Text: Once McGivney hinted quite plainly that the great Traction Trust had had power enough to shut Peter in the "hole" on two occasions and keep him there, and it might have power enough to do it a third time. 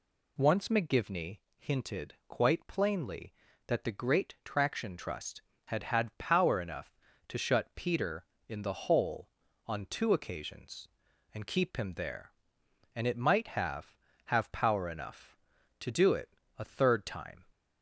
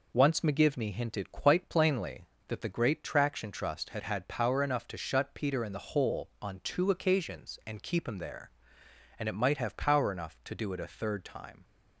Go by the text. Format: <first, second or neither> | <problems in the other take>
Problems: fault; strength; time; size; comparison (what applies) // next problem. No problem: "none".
second | pauses between "McGivney" and "hinted"; slight; at 1.3 s; 0.18 s long // says "have" twice; at 14.3 s // pauses between "it" and "a"; slight; at 16.3 s; 0.24 s long